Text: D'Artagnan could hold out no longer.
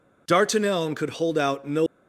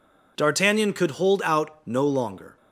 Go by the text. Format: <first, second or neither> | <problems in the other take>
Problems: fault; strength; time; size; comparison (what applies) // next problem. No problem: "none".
second | stops before "longer"; at 1.8 s